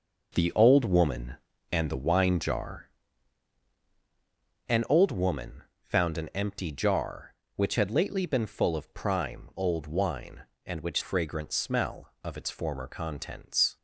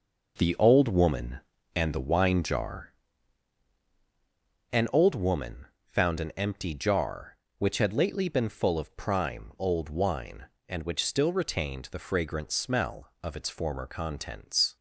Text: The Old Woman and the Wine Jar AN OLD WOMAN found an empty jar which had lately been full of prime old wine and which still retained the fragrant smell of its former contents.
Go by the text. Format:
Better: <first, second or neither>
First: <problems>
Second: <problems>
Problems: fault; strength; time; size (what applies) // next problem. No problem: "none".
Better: second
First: pauses between "Jar" and "AN"; strong; at 2.8 s; 1.7 s long // pauses between "WOMAN" and "found"; slight; at 5.6 s; 0.22 s long // skips "still retained the"; at 11.0 s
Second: pauses between "Jar" and "AN"; strong; at 2.9 s; 1.7 s long // pauses between "WOMAN" and "found"; slight; at 5.6 s; 0.22 s long